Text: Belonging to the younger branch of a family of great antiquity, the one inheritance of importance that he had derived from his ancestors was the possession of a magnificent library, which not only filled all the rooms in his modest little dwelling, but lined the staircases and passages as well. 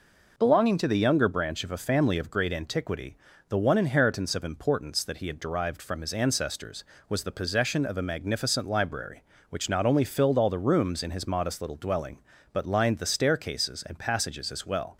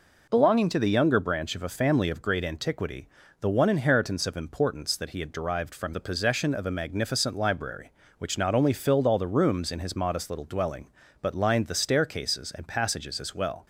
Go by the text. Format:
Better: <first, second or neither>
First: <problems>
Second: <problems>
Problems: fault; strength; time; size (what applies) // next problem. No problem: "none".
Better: first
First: none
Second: skips "his ancestors was"; at 5.9 s